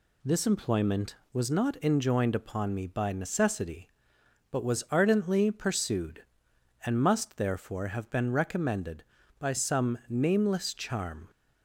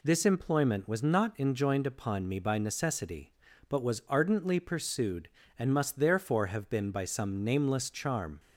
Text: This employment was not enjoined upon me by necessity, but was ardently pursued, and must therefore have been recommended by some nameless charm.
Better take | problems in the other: first | skips "recommended"; at 6.9 s

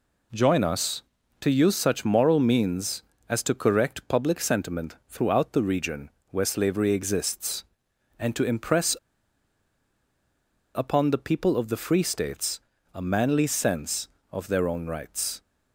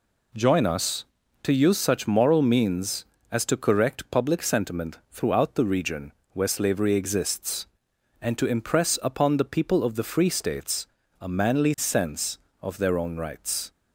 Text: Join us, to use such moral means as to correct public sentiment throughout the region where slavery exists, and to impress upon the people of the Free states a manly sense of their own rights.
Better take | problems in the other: second | pauses between "region" and "where"; slight; at 6.1 s; 0.18 s long; slight in the second // pauses between "impress" and "upon"; strong; at 8.9 s; 1.8 s long // pauses between "states" and "a"; slight; at 12.6 s; 0.32 s long; slight in the second

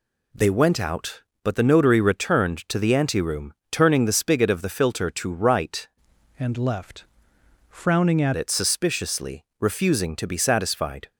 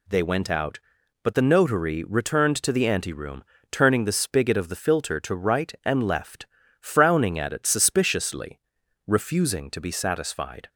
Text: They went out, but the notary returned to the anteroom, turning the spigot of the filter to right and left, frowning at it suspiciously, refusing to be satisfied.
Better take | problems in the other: second | changes voice from "and" to "at"; from 6.3 to 8.3 s; 2.0 s long

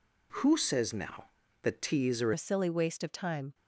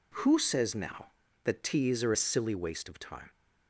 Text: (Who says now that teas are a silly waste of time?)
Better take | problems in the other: second | changes voice at "a"; from 2.3 s on; 1.2 s long

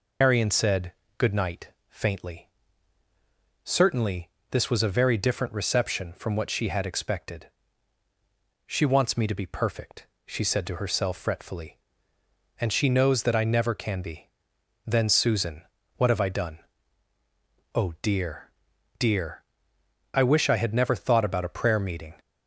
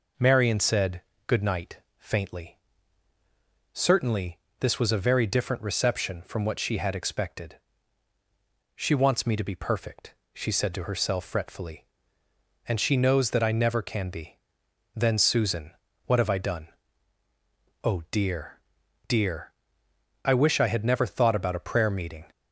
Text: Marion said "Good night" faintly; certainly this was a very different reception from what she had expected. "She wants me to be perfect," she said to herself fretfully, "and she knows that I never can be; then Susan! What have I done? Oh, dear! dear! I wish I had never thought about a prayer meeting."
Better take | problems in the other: second | loses the start of "Marion"; at 0.2 s; 130 ms // pauses between "said" and "Good"; slight; at 0.9 s; 0.26 s long; slight in the second // pauses between "night" and "faintly"; slight; at 1.6 s; 0.20 s long; slight in the second // pauses between "certainly" and "this"; slight; at 4.2 s; 0.22 s long; slight in the second

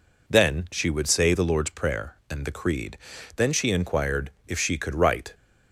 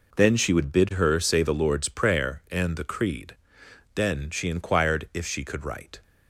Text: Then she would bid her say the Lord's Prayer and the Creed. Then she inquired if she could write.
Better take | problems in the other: second | skips "bid her"; at 1.0 s // pauses between "inquired" and "if"; slight; at 4.3 s; 0.16 s long

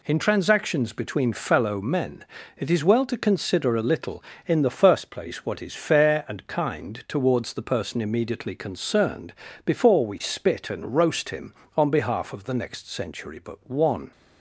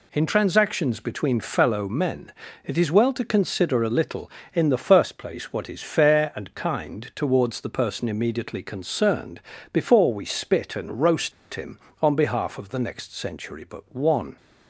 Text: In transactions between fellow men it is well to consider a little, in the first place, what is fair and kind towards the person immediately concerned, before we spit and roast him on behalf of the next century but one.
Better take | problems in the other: first | pauses between "men" and "it"; slight; at 2.3 s; 0.34 s long; slight in the first // pauses between "roast" and "him"; slight; at 11.3 s; 0.22 s long

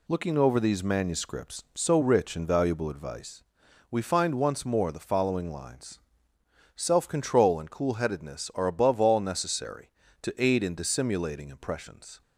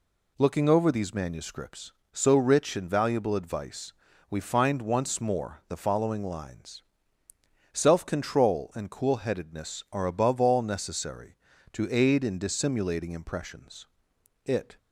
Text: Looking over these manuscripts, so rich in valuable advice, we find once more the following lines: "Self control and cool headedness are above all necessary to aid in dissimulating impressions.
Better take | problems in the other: first | goes on to say "It"; slight; from 14.4 s on; 0.34 s long

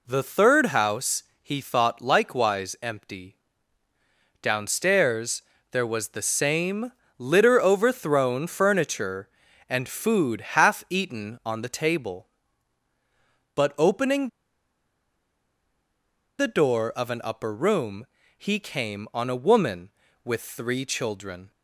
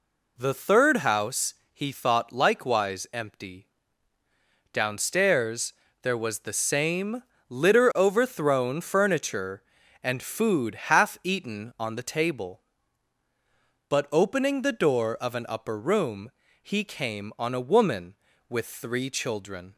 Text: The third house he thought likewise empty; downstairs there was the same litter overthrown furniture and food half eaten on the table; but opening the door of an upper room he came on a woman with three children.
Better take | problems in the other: second | pauses between "house" and "he"; slight; at 1.2 s; 0.18 s long; slight in the second // pauses between "downstairs" and "there"; slight; at 5.4 s; 0.30 s long; slight in the second // pauses between "same" and "litter"; slight; at 6.9 s; 0.26 s long; slight in the second // pauses between "opening" and "the"; strong; at 14.2 s; 2.1 s long // pauses between "room" and "he"; slight; at 18.0 s; 0.32 s long; slight in the second

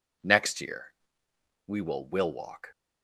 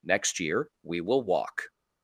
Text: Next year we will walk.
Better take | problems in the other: second | pauses between "year" and "we"; noticeable; at 0.8 s; 0.80 s long // says "will" twice; at 2.0 s

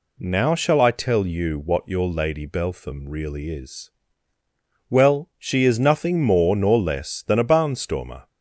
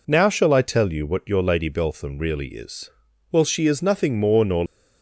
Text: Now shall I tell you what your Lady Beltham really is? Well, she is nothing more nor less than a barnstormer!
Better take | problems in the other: first | stops before "less than a barnstormer"; at 4.6 s

